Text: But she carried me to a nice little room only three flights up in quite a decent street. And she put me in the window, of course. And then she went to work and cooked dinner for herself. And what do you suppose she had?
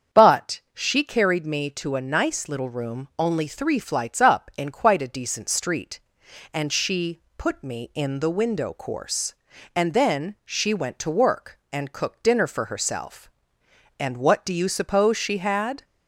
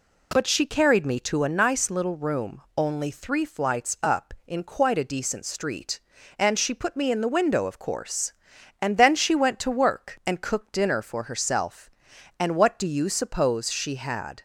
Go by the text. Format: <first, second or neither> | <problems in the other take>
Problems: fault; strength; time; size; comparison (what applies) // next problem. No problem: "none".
second | starts louder than the rest; strong; until 1.2 s; 7.5 dB // pauses between "she" and "put"; slight; at 7.1 s; 0.18 s long // skips "of"; at 8.7 s